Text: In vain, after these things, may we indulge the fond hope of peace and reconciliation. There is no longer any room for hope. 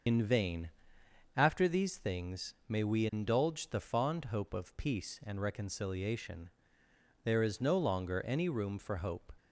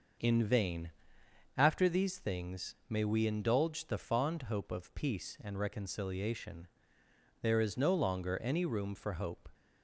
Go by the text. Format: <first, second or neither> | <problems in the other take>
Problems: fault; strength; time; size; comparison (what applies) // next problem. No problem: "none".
second | loses the start of "In"; at 0.0 s; 75 ms // starts louder than the rest; noticeable; until 1.7 s; 6 dB; noticeable in the second